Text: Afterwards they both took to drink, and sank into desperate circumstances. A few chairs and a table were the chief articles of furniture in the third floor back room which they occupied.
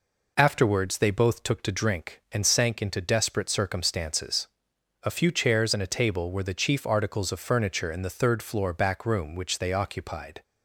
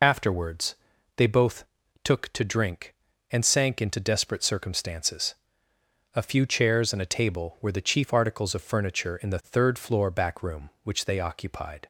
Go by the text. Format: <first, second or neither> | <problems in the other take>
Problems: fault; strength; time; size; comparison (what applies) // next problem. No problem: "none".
first | loses the start of "Afterwards"; at 0.0 s; 45 ms // pauses between "Afterwards" and "they"; at 0.7 s; 0.40 s long // pauses between "both" and "took"; at 1.6 s; 0.40 s long